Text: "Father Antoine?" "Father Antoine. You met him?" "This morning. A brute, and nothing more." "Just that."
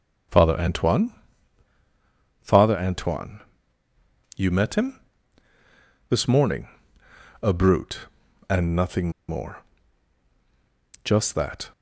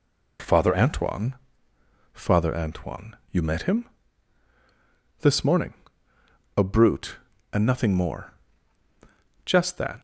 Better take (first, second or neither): second